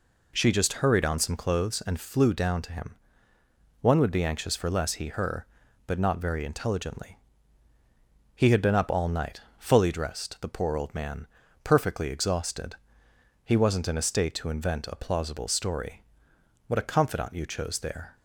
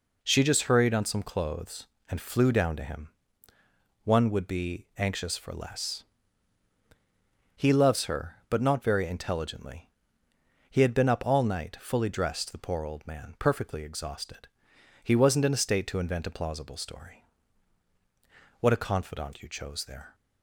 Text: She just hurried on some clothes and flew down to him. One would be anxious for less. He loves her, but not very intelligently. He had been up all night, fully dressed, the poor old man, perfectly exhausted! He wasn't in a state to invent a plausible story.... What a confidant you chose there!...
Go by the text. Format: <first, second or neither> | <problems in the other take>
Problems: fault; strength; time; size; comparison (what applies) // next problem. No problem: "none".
second | skips "loves"; at 5.0 s